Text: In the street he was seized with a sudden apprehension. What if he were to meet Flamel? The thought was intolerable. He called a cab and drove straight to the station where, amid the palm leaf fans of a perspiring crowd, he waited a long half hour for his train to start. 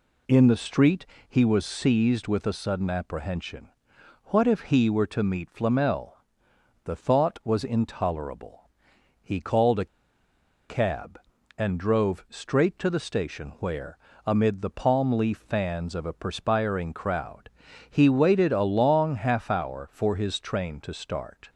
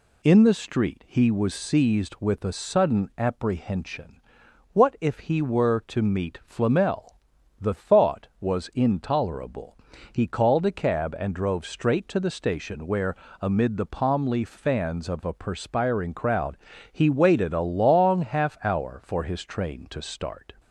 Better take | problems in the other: second | pauses between "street" and "he"; slight; at 1.0 s; 0.22 s long // pauses between "a" and "cab"; noticeable; at 9.8 s; 0.82 s long

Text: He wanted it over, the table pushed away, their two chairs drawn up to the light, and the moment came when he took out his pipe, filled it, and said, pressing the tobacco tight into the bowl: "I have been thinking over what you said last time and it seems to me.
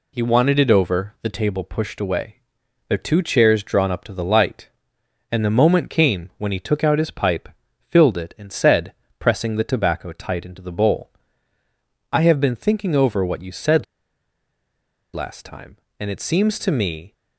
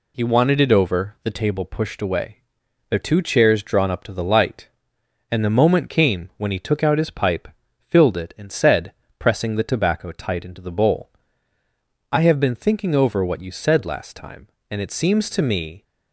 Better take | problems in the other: second | pauses between "said" and "last"; strong; at 13.8 s; 1.3 s long

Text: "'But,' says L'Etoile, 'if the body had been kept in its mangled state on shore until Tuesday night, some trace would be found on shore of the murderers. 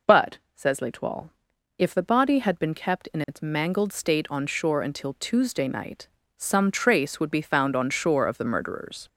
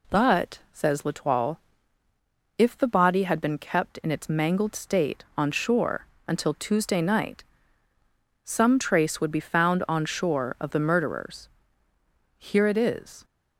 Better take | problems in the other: first | pauses between "shore" and "until"; slight; at 6.0 s; 0.22 s long // goes on to say "Here it is"; noticeable; from 12.3 s on; 0.86 s long

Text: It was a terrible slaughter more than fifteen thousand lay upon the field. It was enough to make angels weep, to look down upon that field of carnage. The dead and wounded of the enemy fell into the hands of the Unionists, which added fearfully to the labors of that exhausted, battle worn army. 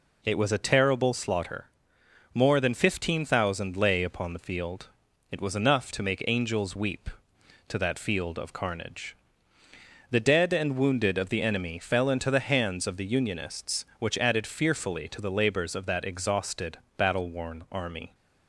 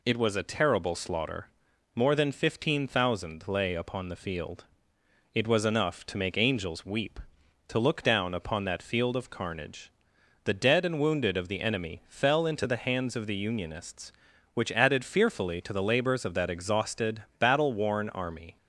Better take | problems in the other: second | pauses between "slaughter" and "more"; noticeable; at 1.6 s; 0.66 s long; noticeable in the second // skips "look down upon"; at 7.7 s

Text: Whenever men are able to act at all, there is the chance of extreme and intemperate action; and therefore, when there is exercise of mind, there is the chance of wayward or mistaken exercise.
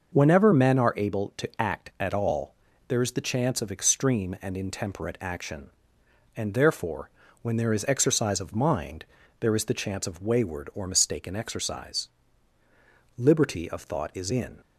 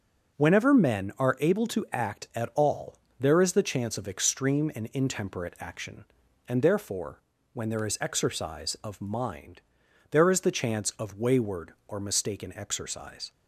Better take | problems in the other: second | goes on to say "Liberty of thought is in"; from 13.1 s on; 1.4 s long

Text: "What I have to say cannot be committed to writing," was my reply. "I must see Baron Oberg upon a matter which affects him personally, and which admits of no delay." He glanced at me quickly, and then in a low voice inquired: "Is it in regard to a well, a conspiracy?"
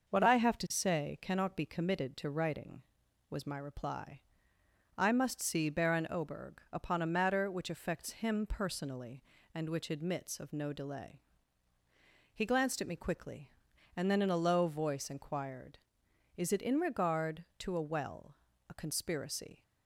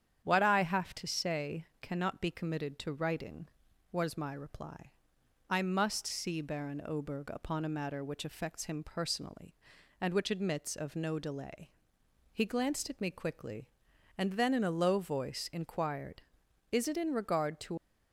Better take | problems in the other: first | starts louder than the rest; strong; until 1.2 s; 9 dB; noticeable in the first // stops before "a well a conspiracy"; at 17.7 s

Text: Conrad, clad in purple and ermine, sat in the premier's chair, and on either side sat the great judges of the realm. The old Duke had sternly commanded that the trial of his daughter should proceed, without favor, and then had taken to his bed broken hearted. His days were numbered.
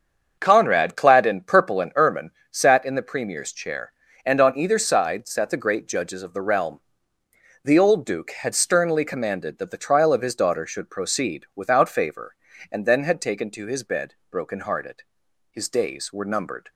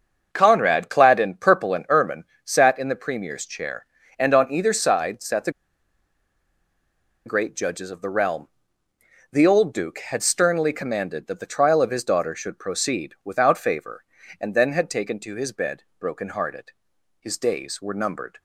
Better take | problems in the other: first | starts louder than the rest; until 1.3 s; 7 dB; also in the first // pauses between "the" and "great"; strong; at 5.5 s; 1.7 s long // pauses between "bed" and "broken"; slight; at 15.8 s; 0.16 s long; slight in the first

